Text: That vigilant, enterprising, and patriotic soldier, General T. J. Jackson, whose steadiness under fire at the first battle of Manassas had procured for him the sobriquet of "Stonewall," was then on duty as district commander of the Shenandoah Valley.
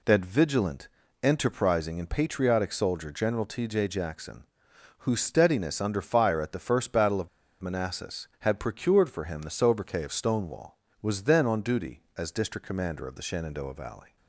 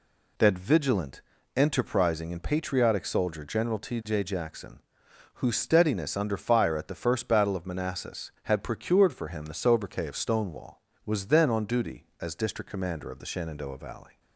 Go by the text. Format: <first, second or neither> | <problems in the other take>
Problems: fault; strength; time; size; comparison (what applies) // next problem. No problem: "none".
second | pauses between "of" and "Manassas"; slight; at 7.2 s; 0.33 s long